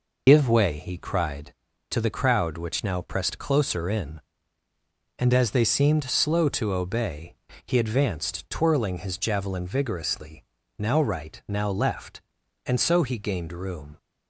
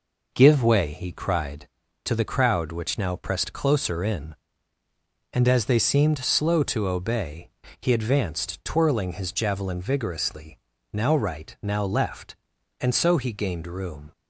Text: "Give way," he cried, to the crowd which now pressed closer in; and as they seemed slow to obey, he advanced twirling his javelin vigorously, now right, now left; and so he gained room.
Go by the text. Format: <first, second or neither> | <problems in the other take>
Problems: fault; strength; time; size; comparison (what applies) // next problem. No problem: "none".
second | loses the start of "Give"; at 0.2 s; 75 ms